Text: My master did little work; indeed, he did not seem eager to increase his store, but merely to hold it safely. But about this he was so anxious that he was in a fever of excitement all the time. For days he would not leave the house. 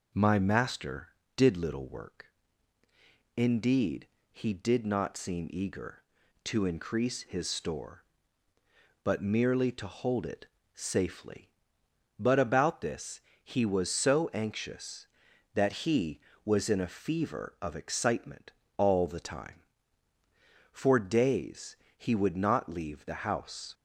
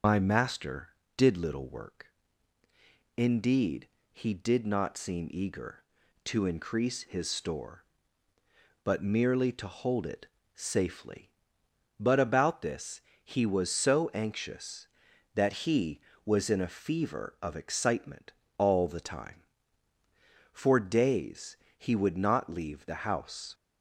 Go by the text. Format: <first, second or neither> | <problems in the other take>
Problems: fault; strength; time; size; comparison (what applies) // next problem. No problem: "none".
first | loses the start of "My"; at 0.0 s; 105 ms // starts louder than the rest; until 1.3 s; 6.5 dB // pauses between "it" and "safely"; slight; at 10.2 s; 0.30 s long; slight in the first // pauses between "this" and "he"; slight; at 13.0 s; 0.22 s long; slight in the first // pauses between "excitement" and "all"; slight; at 18.3 s; 0.26 s long; slight in the first // pauses between "days" and "he"; slight; at 21.5 s; 0.22 s long; slight in the first